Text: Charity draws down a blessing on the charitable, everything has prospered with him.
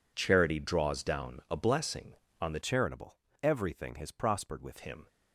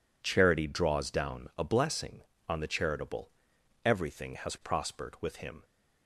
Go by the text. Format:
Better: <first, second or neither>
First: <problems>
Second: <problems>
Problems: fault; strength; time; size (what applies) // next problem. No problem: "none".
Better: second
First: changes voice from "charitable" to "with"; from 2.6 to 4.7 s; 2.1 s long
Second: none